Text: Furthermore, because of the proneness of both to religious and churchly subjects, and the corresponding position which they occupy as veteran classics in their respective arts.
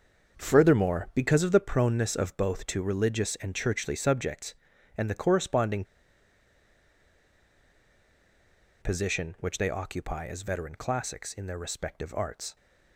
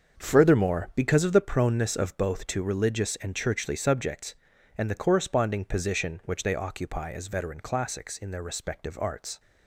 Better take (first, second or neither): second